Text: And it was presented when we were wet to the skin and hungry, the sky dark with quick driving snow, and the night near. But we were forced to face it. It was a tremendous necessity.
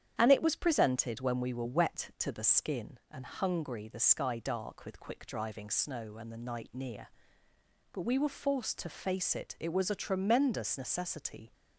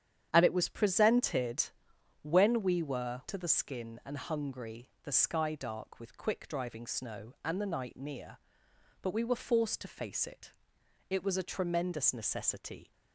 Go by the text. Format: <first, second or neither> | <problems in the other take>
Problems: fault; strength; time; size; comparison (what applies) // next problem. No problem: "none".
first | starts louder than the rest; strong; until 1.3 s; 9.5 dB; strong in the first // pauses between "presented" and "when"; noticeable; at 1.6 s; 0.56 s long // skips "wet"; at 3.2 s